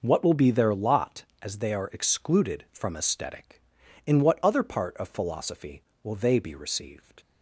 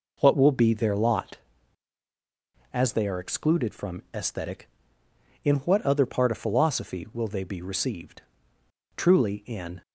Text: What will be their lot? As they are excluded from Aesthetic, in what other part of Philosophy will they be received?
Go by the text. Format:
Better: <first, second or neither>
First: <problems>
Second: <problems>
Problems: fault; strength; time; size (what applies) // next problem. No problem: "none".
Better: first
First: none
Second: goes on to say "Truly in"; noticeable; from 8.9 s on; 0.86 s long